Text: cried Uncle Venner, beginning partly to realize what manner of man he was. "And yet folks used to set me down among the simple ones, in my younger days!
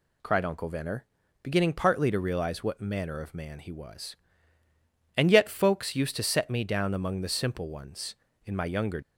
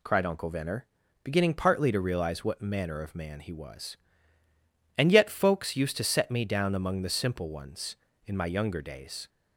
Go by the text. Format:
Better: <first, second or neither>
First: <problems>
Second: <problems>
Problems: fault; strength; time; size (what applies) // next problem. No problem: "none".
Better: second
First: stops before "days"; at 9.0 s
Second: none